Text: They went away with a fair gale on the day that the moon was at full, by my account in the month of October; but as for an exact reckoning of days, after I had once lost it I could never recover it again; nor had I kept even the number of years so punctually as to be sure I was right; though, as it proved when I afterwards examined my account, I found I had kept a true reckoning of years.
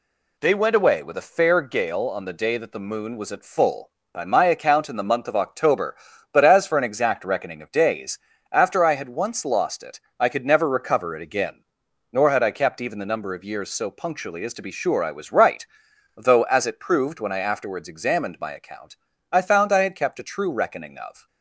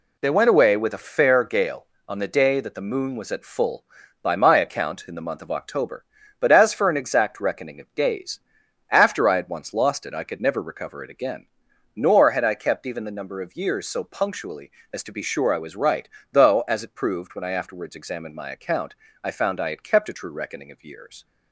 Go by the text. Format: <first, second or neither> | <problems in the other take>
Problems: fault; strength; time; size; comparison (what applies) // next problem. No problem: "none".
second | pauses between "it" and "I"; slight; at 9.9 s; 0.20 s long // stops before "years"; at 21.2 s